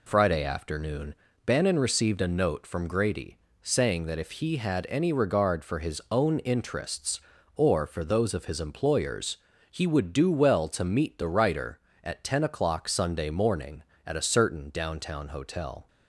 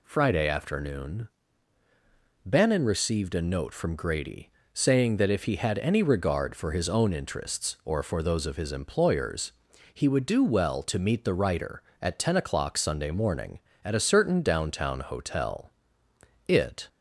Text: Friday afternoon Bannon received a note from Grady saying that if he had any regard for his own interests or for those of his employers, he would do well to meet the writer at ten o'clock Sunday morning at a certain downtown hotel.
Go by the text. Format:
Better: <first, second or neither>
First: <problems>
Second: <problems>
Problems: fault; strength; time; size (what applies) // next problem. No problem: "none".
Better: first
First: pauses between "afternoon" and "Bannon"; slight; at 1.1 s; 0.30 s long // pauses between "Grady" and "saying"; slight; at 3.3 s; 0.26 s long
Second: pauses between "afternoon" and "Bannon"; at 1.2 s; 1.1 s long // pauses between "Grady" and "saying"; slight; at 4.5 s; 0.22 s long // goes on to say "It"; slight; from 16.4 s on; 0.40 s long